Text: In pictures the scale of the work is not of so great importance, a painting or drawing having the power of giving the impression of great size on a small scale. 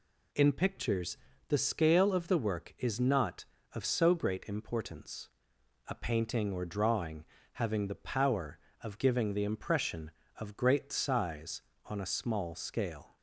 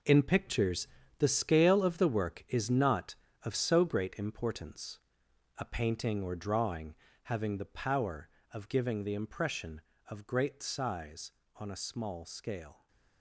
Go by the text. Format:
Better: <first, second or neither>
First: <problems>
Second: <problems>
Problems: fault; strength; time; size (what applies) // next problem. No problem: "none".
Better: first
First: pauses between "pictures" and "the"; slight; at 1.1 s; 0.32 s long // pauses between "drawing" and "having"; slight; at 7.2 s; 0.30 s long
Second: gets quieter; strong; throughout; 10.5 dB // pauses between "pictures" and "the"; slight; at 0.8 s; 0.32 s long // pauses between "drawing" and "having"; slight; at 6.9 s; 0.30 s long